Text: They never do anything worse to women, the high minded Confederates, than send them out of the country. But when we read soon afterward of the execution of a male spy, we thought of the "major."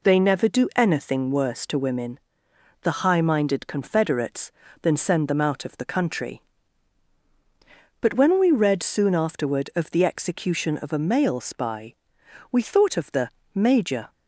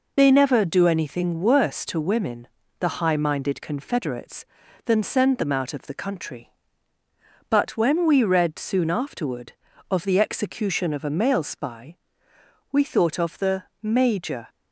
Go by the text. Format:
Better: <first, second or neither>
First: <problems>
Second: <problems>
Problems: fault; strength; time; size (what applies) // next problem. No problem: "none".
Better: first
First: pauses between "the" and "major"; slight; at 13.2 s; 0.26 s long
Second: loses the start of "They"; at 0.1 s; 30 ms // pauses between "the" and "major"; slight; at 13.6 s; 0.18 s long